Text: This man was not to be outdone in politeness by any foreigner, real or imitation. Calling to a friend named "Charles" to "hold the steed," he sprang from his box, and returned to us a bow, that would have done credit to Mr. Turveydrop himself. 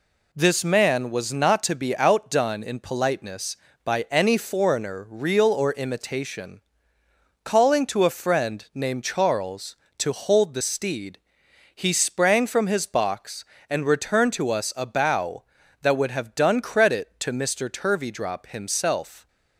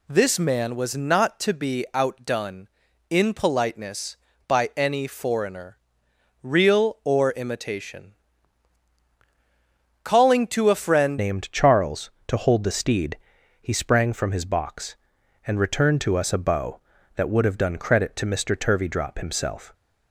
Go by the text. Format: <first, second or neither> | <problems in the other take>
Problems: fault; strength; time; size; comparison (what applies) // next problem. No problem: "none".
first | changes voice at "named"; from 11.1 s on; 8.6 s long